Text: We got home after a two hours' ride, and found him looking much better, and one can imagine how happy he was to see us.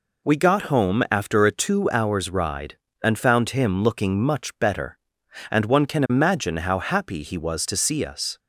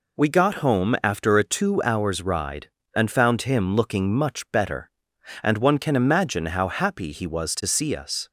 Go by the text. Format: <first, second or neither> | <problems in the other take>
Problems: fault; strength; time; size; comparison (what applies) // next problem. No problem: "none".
neither | none